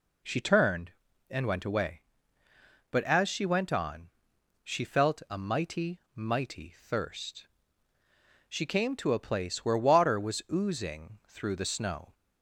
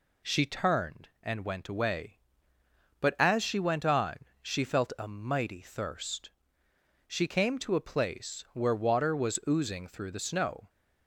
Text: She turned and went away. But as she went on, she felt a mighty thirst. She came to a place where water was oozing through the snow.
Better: second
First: says "mighty" twice; at 6.1 s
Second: none

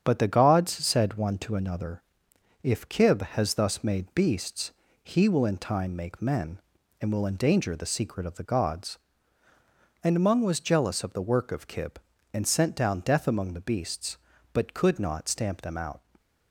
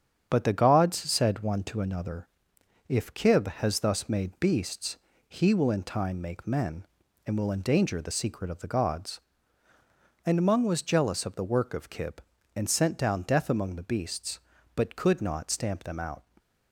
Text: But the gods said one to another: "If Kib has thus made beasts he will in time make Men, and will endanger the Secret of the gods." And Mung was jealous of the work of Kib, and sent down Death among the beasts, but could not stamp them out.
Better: neither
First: starts louder than the rest; strong; until 1.0 s; 8 dB // pauses between "beasts" and "he"; slight; at 4.7 s; 0.28 s long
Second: starts louder than the rest; strong; until 1.2 s; 8 dB // pauses between "beasts" and "he"; slight; at 4.9 s; 0.28 s long

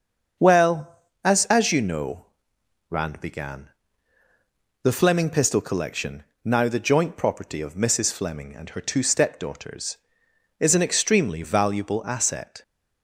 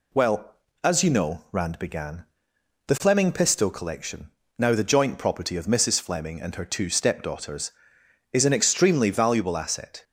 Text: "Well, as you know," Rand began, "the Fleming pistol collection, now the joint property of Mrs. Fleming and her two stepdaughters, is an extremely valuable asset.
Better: second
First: starts louder than the rest; until 1.6 s; 6.5 dB // says "as" twice; at 1.4 s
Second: none

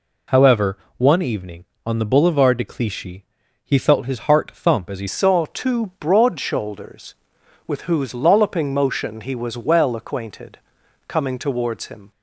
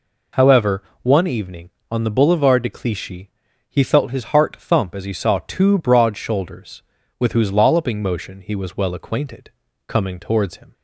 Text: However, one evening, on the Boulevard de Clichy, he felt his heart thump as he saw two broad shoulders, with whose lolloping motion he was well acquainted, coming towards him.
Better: second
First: changes voice at "saw"; from 5.0 s on; 7.1 s long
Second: none

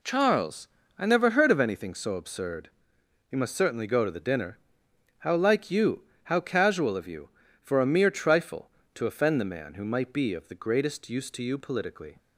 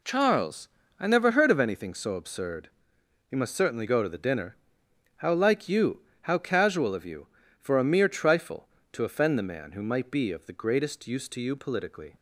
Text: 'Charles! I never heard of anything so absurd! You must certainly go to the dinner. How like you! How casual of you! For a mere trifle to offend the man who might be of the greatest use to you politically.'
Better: neither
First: none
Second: none

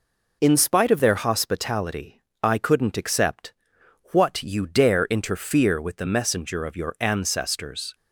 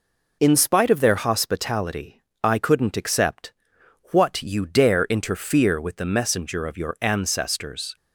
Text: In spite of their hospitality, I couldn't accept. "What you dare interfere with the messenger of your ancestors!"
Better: neither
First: none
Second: none

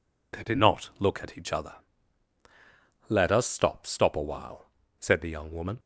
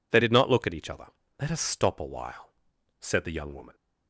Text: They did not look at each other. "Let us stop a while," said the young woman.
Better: second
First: says "stop" twice; at 3.8 s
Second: none

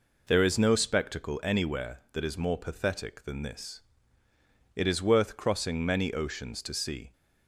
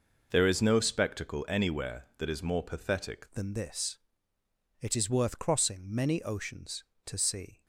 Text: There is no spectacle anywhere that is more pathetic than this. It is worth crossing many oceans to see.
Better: first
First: none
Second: changes voice at "than"; from 3.3 s on; 4.3 s long

